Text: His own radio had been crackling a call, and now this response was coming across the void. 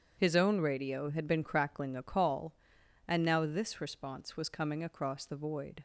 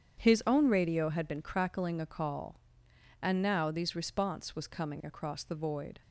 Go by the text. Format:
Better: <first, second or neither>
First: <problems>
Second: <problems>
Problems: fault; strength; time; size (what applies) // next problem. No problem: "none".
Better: first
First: starts louder than the rest; strong; until 1.1 s; 8 dB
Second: starts louder than the rest; strong; until 1.2 s; 8 dB // says "these" for "this"; at 3.7 s